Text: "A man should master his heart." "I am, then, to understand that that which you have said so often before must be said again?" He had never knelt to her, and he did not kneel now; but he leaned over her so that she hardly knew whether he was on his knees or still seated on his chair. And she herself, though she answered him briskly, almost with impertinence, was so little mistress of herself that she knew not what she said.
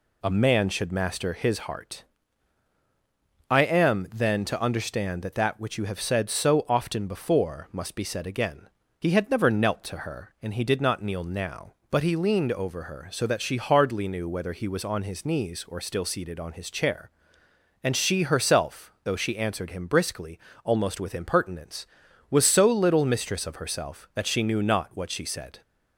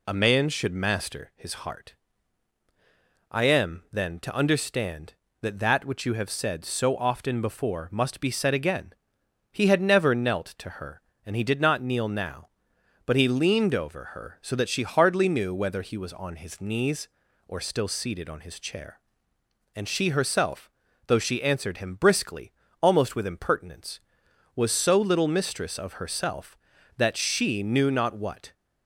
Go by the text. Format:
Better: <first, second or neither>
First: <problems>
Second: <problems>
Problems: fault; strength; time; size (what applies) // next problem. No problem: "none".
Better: first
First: none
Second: stops before "she said"; at 28.5 s